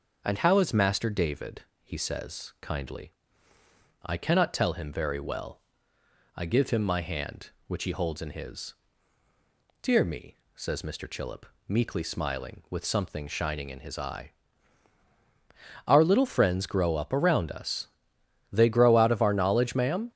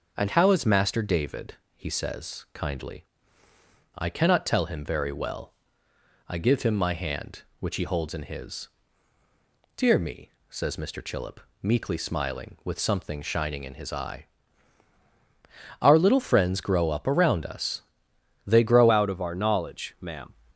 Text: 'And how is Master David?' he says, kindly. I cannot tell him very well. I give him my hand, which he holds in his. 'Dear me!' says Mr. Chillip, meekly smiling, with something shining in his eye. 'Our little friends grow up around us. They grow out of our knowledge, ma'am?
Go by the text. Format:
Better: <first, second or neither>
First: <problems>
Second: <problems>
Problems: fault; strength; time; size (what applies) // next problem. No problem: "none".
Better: first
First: starts louder than the rest; until 1.2 s; 6.5 dB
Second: starts louder than the rest; until 1.1 s; 6.5 dB // changes voice at "out"; from 18.8 s on; 1.5 s long